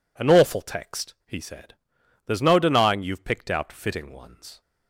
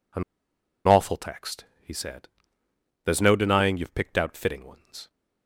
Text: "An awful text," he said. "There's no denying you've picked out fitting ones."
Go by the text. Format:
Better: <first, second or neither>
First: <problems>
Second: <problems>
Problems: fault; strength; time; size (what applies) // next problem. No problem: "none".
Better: first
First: none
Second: pauses between "An" and "awful"; noticeable; at 0.2 s; 0.64 s long